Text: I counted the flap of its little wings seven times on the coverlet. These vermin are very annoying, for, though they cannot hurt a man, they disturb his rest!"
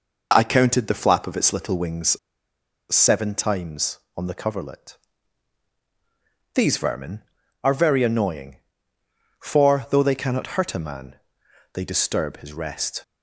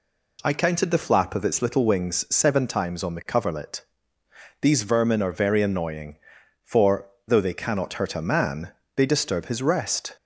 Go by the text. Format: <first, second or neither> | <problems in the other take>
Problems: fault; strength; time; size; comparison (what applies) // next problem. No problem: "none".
second | pauses between "wings" and "seven"; noticeable; at 2.1 s; 0.78 s long